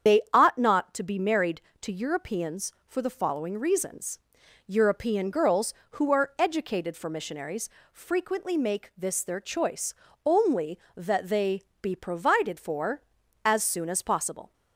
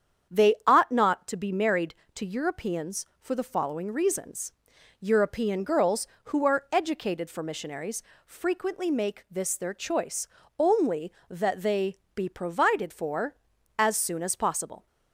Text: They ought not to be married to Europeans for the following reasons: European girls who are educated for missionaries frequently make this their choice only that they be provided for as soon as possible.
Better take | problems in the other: second | loses the start of "They"; at 0.0 s; 90 ms // starts louder than the rest; strong; until 1.2 s; 8 dB; strong in the second // pauses between "missionaries" and "frequently"; slight; at 7.6 s; 0.22 s long; slight in the second // pauses between "choice" and "only"; slight; at 9.9 s; 0.32 s long; slight in the second // pauses between "they" and "be"; slight; at 11.6 s; 0.18 s long; slight in the second

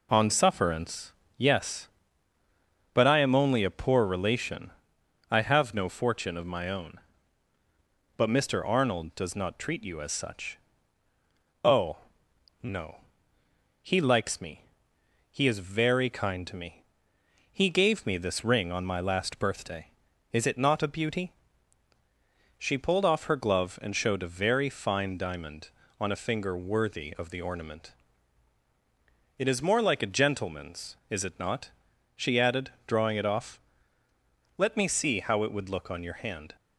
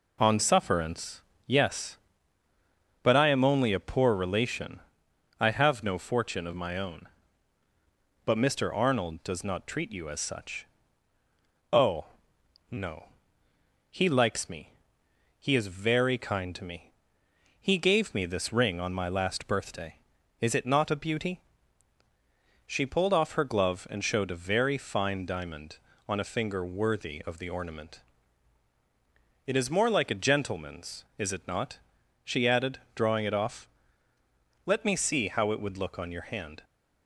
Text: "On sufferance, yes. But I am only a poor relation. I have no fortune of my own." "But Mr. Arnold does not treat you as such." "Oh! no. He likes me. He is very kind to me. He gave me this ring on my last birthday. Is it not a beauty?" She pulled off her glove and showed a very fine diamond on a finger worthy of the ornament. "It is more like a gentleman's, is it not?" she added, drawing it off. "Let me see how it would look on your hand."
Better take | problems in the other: neither | none

